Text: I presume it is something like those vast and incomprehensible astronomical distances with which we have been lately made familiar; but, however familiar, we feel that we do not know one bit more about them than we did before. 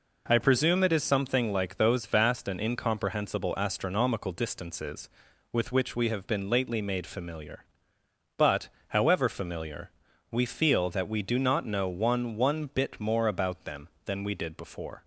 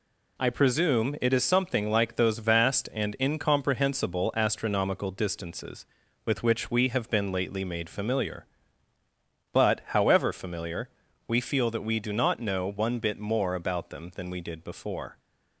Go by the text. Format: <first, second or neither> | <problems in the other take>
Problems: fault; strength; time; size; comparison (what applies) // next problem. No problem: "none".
second | says "one" twice; at 12.3 s